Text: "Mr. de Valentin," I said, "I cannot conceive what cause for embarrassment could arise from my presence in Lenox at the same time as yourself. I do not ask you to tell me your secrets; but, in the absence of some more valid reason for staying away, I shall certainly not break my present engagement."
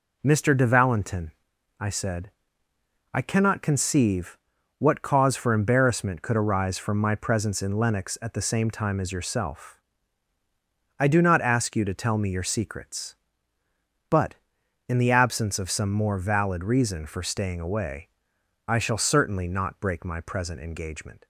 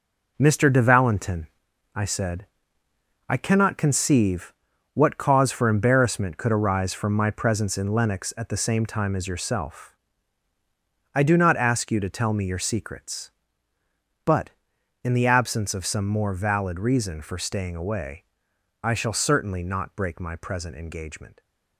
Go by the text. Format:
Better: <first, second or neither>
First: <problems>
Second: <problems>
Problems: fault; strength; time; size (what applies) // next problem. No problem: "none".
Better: first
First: pauses between "conceive" and "what"; at 4.3 s; 0.40 s long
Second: gets quieter; strong; throughout; 8.5 dB // pauses between "conceive" and "what"; at 4.5 s; 0.40 s long